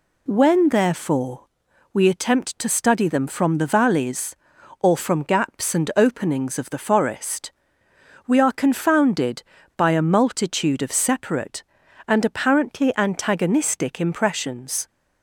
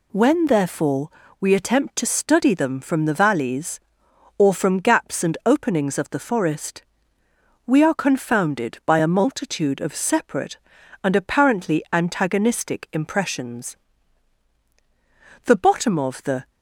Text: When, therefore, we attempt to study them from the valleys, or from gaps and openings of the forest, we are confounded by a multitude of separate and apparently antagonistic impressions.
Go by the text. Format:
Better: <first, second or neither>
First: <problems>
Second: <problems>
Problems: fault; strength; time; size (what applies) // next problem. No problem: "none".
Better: first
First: none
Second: goes on to say "The bottom of the"; noticeable; from 15.4 s on; 1.0 s long